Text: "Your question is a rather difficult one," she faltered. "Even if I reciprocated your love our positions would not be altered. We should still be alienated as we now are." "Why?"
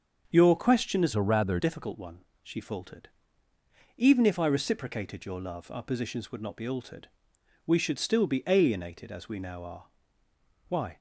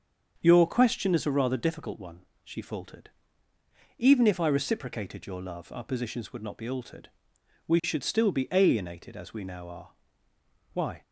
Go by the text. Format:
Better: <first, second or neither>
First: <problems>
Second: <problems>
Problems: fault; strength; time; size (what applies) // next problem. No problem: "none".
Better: second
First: starts louder than the rest; until 1.3 s; 6.5 dB // changes voice from "a" to "rather"; from 1.1 to 1.5 s; 0.4 s long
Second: starts louder than the rest; until 1.4 s; 7 dB